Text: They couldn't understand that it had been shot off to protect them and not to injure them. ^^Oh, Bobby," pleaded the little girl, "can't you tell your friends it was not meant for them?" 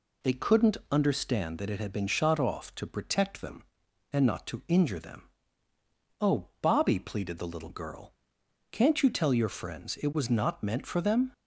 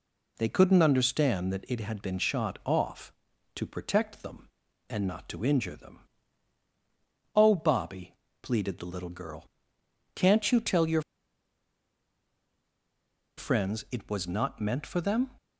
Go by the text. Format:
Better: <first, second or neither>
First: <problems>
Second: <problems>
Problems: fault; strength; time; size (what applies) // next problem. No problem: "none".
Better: first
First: none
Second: pauses between "your" and "friends"; strong; at 11.0 s; 2.3 s long